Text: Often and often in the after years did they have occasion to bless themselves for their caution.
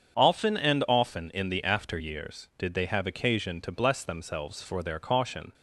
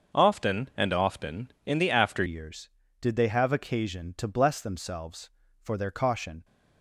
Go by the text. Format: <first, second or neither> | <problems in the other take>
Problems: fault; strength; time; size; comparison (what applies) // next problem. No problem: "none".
first | starts louder than the rest; until 1.2 s; 6.5 dB; strong in the first // changes voice at "years"; from 2.2 s on; 4.2 s long